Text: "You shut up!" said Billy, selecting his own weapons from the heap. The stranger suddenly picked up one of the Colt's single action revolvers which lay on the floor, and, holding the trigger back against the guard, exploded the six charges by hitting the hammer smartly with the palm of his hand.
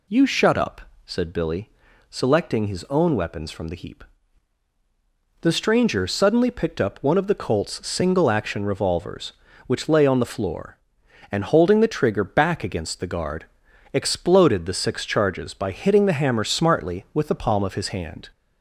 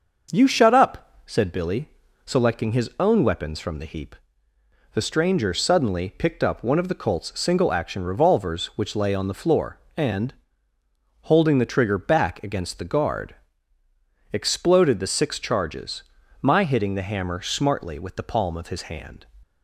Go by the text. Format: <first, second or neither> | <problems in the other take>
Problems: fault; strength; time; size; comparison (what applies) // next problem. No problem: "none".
first | starts louder than the rest; until 1.4 s; 6 dB // says "my" for "by"; at 16.4 s